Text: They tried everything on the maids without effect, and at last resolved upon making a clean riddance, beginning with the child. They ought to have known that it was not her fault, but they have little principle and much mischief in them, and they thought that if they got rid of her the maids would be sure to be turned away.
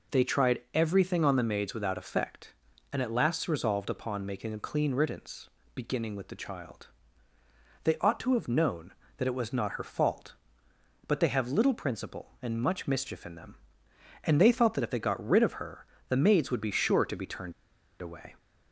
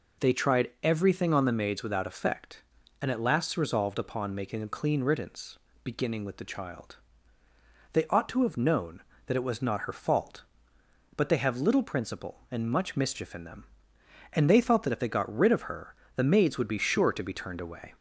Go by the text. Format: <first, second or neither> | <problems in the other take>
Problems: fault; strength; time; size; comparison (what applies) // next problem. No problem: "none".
second | pauses between "her" and "the"; slight; at 15.8 s; 0.24 s long; slight in the second // pauses between "turned" and "away"; noticeable; at 17.5 s; 0.48 s long